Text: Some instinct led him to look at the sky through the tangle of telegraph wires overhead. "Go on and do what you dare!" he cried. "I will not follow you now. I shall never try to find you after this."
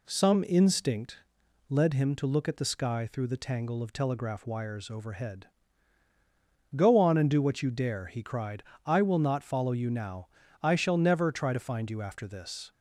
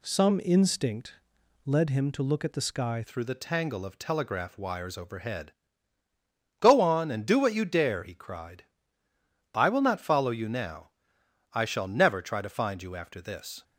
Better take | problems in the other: first | pauses between "instinct" and "led"; noticeable; at 1.1 s; 0.50 s long; noticeable in the first // changes voice at "through"; from 3.0 s on; 10.6 s long

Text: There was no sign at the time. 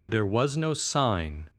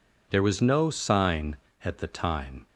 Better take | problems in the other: second | stops before "at the time"; at 1.4 s

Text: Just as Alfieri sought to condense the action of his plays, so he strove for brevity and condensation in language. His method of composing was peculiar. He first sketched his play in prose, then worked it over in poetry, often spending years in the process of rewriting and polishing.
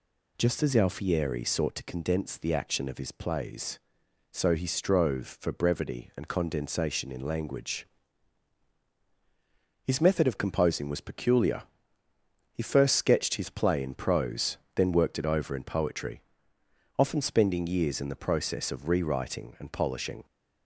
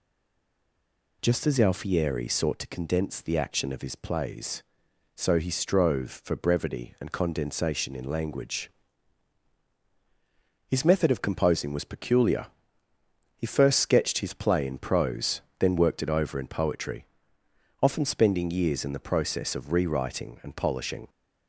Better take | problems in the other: first | stays silent before the first word; noticeable; until 1.2 s; 1.2 s long

